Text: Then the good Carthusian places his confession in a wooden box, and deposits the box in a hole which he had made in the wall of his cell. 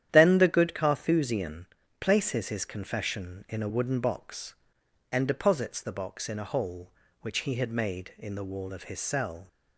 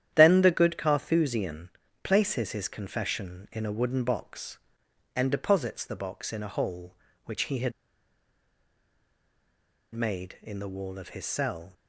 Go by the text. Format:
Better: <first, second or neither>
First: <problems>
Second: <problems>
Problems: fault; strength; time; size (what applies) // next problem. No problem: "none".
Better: first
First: starts louder than the rest; strong; until 1.1 s; 10.5 dB // pauses between "Carthusian" and "places"; slight; at 1.6 s; 0.34 s long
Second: starts louder than the rest; strong; until 1.1 s; 10.5 dB // pauses between "Carthusian" and "places"; slight; at 1.6 s; 0.34 s long // pauses between "had" and "made"; strong; at 7.7 s; 2.2 s long